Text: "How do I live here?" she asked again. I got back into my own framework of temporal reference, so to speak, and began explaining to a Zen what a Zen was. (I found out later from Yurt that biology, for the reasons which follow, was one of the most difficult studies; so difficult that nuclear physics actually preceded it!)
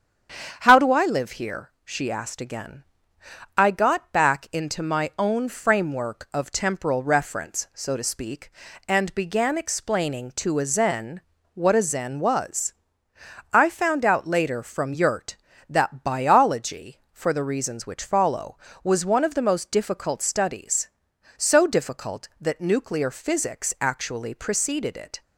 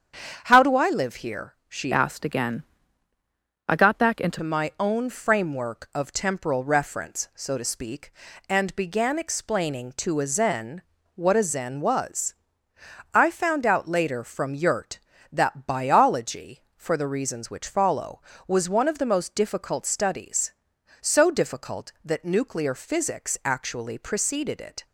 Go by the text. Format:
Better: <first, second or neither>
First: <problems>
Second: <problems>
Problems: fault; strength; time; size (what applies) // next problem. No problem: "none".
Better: first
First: starts louder than the rest; strong; until 1.6 s; 8 dB // pauses between "Zen" and "what"; slight; at 11.2 s; 0.34 s long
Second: starts louder than the rest; strong; until 1.4 s; 8 dB // changes voice from "asked" to "into"; from 1.9 to 4.3 s; 2.4 s long // pauses between "Zen" and "what"; slight; at 10.8 s; 0.34 s long